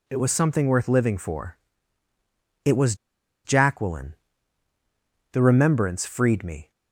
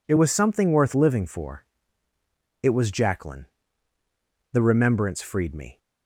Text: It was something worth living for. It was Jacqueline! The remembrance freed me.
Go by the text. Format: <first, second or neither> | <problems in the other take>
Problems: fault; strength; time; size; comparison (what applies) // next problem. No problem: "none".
second | pauses between "was" and "Jacqueline"; noticeable; at 2.9 s; 0.50 s long